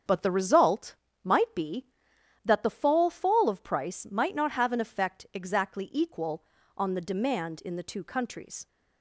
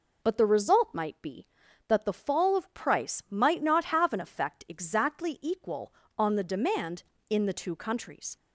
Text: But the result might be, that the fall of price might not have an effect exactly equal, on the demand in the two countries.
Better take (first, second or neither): second